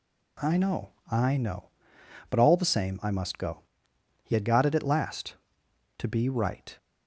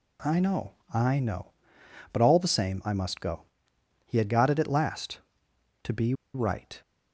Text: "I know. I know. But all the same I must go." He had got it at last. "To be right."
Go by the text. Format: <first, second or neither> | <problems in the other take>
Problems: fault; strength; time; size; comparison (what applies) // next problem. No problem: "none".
first | pauses between "be" and "right"; slight; at 6.1 s; 0.21 s long